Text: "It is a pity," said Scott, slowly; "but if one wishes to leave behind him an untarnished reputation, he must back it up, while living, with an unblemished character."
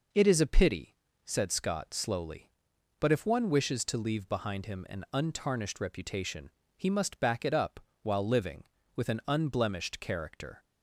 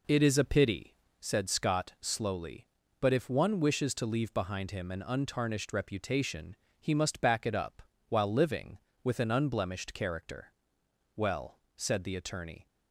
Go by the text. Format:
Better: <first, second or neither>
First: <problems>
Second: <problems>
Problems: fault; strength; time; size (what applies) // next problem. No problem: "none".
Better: first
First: none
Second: goes on to say "Well said the attorney"; from 11.1 s on; 1.5 s long